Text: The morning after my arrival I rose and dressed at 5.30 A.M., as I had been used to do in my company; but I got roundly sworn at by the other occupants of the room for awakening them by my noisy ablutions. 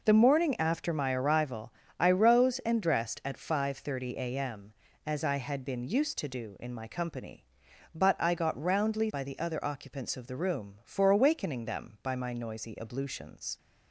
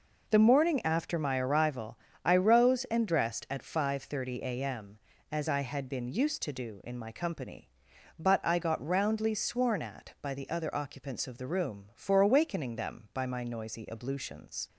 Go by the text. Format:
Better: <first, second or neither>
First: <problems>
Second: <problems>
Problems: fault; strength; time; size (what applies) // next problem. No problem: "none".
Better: second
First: pauses between "arrival" and "I"; slight; at 1.7 s; 0.28 s long // skips "sworn at"; at 9.1 s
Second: pauses between "arrival" and "I"; slight; at 1.9 s; 0.28 s long